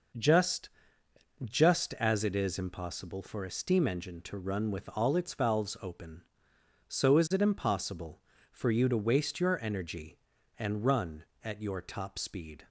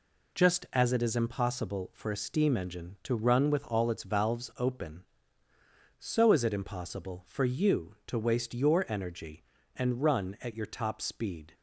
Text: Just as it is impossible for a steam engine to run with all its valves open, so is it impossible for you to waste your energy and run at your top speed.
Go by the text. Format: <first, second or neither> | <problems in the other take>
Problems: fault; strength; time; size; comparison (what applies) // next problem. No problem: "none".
second | says "Just" twice; at 1.4 s